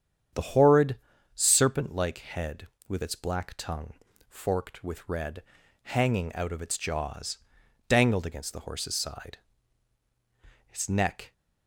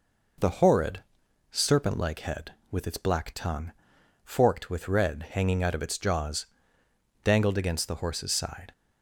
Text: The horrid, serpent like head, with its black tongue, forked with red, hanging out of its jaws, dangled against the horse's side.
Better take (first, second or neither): second